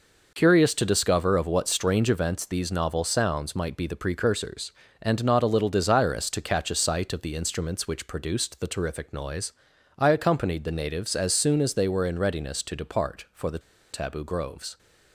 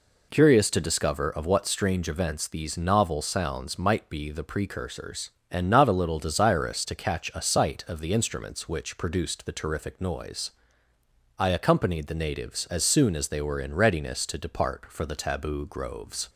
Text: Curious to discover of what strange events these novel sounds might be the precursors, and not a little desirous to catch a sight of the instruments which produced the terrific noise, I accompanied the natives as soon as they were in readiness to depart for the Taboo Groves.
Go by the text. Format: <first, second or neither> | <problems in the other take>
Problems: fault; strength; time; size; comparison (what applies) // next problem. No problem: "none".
second | pauses between "the" and "Taboo"; slight; at 13.5 s; 0.33 s long